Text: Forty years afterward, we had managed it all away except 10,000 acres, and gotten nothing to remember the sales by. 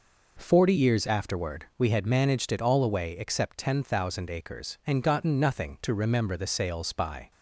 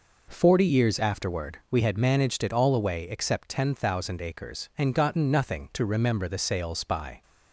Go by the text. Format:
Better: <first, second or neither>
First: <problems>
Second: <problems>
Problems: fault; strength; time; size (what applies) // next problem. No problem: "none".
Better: neither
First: none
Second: none